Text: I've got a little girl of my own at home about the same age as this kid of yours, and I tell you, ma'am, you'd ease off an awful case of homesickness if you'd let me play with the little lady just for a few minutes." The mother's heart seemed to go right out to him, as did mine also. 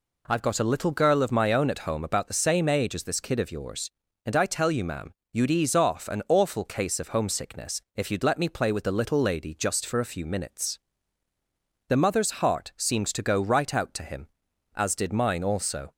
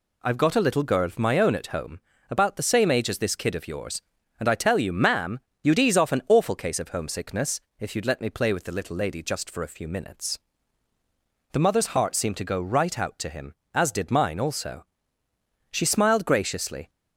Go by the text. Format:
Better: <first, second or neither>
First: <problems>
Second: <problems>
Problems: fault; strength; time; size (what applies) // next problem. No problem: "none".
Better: first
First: none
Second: pauses between "home" and "about"; slight; at 1.9 s; 0.30 s long // pauses between "homesickness" and "if"; slight; at 7.6 s; 0.18 s long // goes on to say "She smiled graciously"; noticeable; from 15.7 s on; 1.1 s long